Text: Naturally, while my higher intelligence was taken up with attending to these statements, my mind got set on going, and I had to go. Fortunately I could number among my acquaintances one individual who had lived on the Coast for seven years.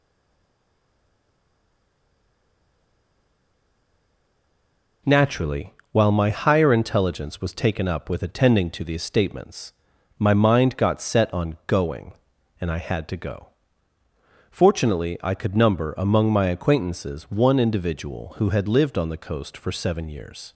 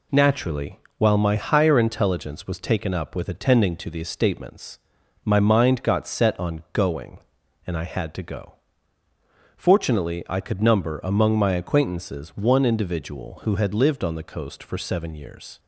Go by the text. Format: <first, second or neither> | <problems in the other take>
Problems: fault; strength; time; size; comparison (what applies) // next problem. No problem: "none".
second | stays silent before the first word; strong; until 5.0 s; 5.0 s long